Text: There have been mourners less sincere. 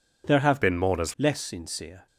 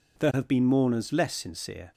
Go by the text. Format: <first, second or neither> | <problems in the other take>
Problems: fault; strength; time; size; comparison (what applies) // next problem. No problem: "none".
second | changes voice from "been" to "mourners"; from 0.6 to 1.1 s; 0.5 s long